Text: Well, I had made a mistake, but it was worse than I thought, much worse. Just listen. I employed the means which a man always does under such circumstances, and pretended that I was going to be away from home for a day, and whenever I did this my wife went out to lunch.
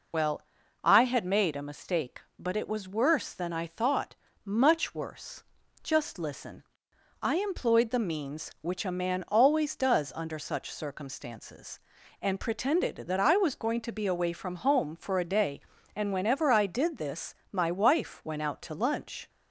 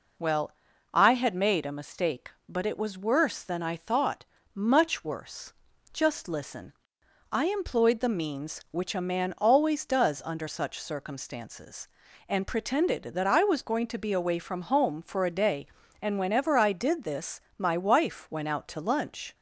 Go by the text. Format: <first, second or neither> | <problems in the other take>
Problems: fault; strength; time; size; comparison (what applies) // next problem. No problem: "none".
second | loses the start of "Well"; at 0.1 s; 50 ms // pauses between "this" and "my"; slight; at 17.3 s; 0.18 s long; slight in the second